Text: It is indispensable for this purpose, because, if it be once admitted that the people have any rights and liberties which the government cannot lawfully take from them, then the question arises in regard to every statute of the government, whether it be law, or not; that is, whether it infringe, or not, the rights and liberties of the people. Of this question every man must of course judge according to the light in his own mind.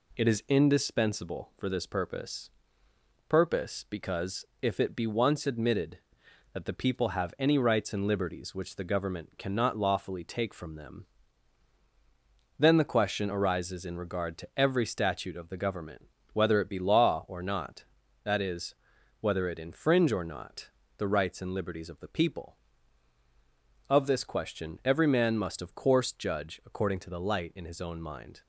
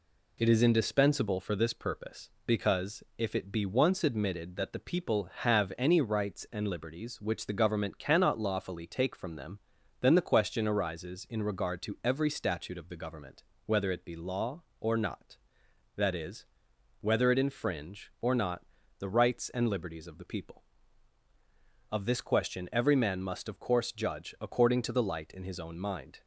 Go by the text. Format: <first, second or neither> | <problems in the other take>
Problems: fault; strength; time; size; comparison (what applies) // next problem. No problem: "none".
second | says "purpose" twice; at 3.2 s